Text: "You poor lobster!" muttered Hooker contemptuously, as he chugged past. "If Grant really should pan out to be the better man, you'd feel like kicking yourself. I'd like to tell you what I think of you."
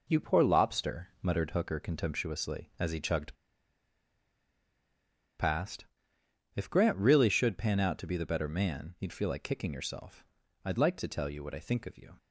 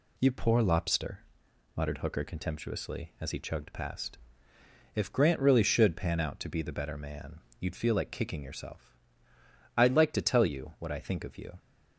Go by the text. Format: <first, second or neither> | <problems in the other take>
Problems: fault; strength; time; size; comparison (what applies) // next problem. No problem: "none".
second | pauses between "chugged" and "past"; strong; at 3.3 s; 2.0 s long